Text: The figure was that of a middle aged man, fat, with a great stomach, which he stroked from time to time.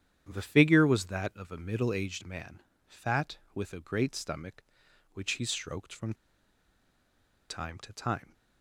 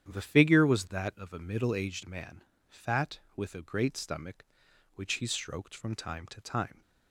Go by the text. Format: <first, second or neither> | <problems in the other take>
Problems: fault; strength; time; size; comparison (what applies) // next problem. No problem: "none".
second | starts louder than the rest; strong; until 1.3 s; 9.5 dB; strong in the second // pauses between "from" and "time"; strong; at 6.1 s; 1.3 s long